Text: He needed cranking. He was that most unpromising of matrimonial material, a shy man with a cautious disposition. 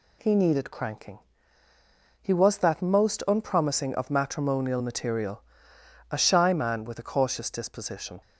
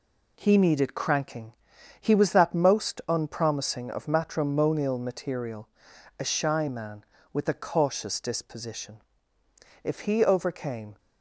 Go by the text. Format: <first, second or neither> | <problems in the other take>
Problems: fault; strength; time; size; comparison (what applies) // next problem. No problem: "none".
first | goes on to say "If he overcame"; noticeable; from 9.8 s on; 1.1 s long